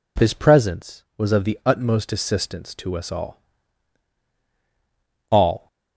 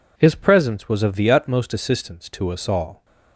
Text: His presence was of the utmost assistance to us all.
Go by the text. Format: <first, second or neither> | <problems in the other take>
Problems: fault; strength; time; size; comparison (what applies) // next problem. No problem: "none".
second | says "all" twice; at 5.3 s